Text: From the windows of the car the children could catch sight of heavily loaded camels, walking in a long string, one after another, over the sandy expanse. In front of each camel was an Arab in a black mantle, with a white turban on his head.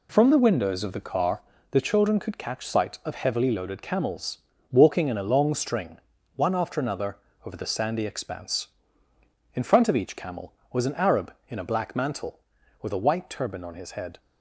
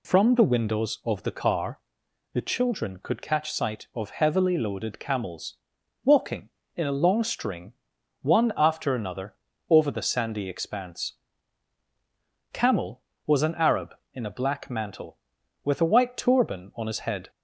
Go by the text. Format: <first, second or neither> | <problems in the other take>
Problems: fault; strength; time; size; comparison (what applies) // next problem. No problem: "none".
first | pauses between "car" and "the"; noticeable; at 1.7 s; 0.52 s long; slight in the first // skips "In front of each"; at 11.8 s